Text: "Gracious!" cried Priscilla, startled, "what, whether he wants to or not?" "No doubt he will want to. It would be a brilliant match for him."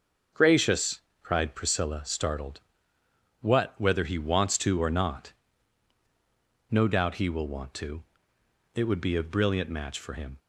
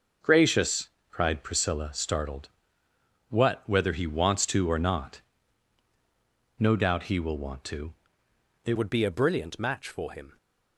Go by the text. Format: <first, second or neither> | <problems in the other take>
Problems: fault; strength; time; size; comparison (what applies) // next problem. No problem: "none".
first | changes voice at "would"; from 8.7 s on; 1.6 s long